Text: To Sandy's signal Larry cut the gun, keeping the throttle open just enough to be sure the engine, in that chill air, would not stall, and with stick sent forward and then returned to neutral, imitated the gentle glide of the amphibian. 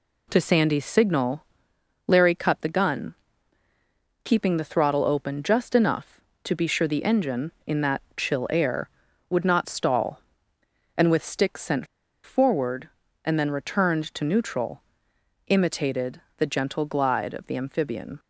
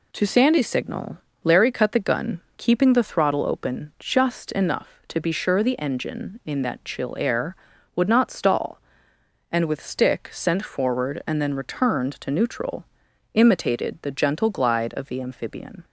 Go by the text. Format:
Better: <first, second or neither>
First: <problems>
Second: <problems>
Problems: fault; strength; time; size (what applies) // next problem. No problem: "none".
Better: second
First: pauses between "signal" and "Larry"; noticeable; at 1.4 s; 0.60 s long // pauses between "that" and "chill"; slight; at 8.0 s; 0.16 s long // pauses between "sent" and "forward"; at 11.8 s; 0.38 s long // pauses between "imitated" and "the"; slight; at 16.2 s; 0.16 s long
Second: pauses between "signal" and "Larry"; slight; at 1.1 s; 0.24 s long